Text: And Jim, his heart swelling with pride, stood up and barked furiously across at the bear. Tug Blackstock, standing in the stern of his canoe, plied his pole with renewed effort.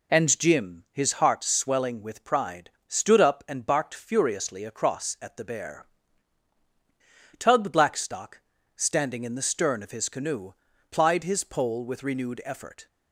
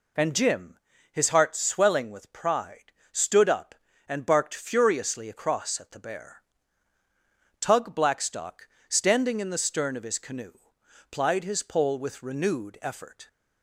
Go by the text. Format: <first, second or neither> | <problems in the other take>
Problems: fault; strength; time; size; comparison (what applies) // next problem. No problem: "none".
neither | none